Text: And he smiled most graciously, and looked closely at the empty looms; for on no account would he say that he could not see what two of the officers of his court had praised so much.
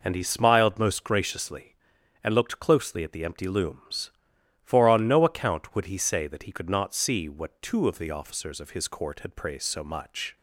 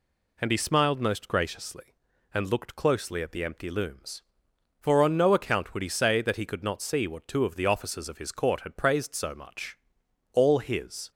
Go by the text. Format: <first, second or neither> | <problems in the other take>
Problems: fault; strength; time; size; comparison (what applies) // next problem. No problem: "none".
first | goes on to say "All his"; noticeable; from 10.3 s on; 0.78 s long